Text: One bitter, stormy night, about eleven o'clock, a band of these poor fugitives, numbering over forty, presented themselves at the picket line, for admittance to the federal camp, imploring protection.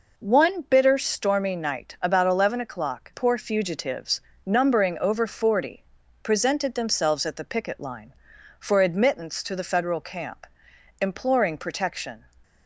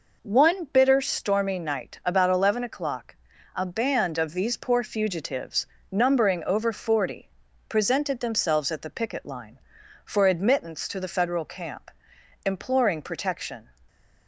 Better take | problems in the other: second | skips "a band of these"; at 3.1 s

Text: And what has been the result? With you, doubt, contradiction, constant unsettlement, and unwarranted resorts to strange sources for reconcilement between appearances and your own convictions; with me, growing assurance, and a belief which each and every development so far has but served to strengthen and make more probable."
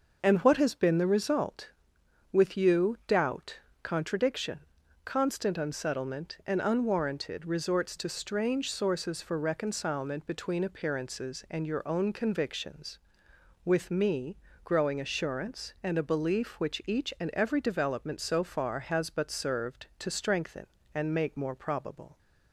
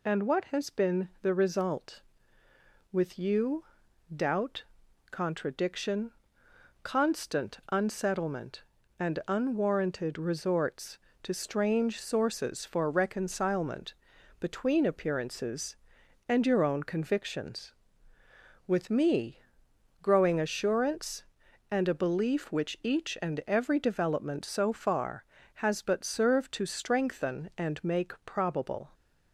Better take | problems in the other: first | pauses between "reconcilement" and "between"; noticeable; at 13.9 s; 0.46 s long // skips "more"; at 28.1 s

